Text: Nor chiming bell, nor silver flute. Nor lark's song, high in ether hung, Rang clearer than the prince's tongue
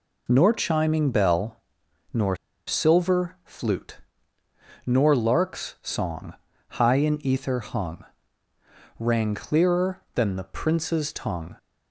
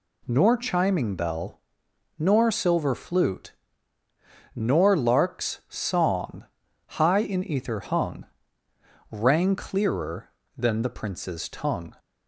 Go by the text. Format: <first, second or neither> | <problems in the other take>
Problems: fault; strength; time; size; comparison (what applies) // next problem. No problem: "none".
second | pauses between "nor" and "silver"; slight; at 2.3 s; 0.31 s long